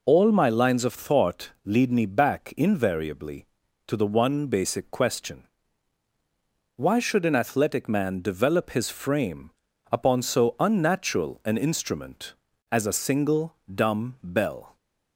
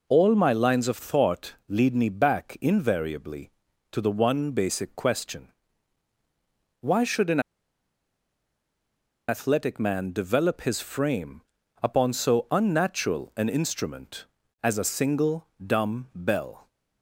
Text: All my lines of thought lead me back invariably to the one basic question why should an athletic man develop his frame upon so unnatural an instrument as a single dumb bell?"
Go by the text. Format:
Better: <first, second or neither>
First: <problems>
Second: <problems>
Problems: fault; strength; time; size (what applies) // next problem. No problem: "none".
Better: first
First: pauses between "thought" and "lead"; slight; at 1.5 s; 0.16 s long // pauses between "question" and "why"; strong; at 5.4 s; 1.3 s long // pauses between "frame" and "upon"; at 9.5 s; 0.40 s long // pauses between "single" and "dumb"; slight; at 13.5 s; 0.18 s long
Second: pauses between "thought" and "lead"; slight; at 1.5 s; 0.16 s long // pauses between "question" and "why"; strong; at 5.4 s; 1.3 s long // pauses between "an" and "athletic"; strong; at 7.3 s; 1.8 s long // pauses between "frame" and "upon"; at 11.4 s; 0.40 s long // pauses between "single" and "dumb"; slight; at 15.4 s; 0.18 s long